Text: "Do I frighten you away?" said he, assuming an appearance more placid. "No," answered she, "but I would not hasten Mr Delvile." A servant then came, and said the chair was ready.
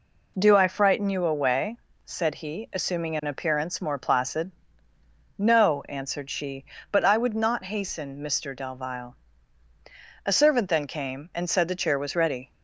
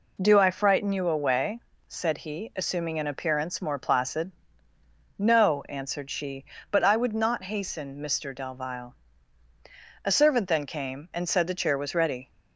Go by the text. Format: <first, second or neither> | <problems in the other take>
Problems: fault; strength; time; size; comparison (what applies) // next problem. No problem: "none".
neither | none